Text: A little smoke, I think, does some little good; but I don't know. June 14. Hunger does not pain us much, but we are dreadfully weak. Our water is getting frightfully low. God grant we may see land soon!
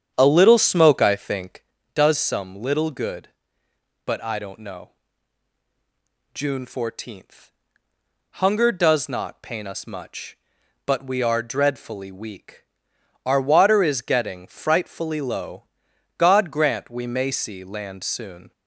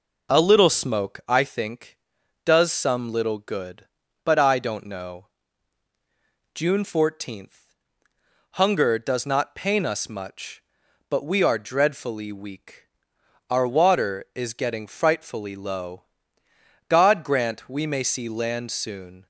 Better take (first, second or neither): second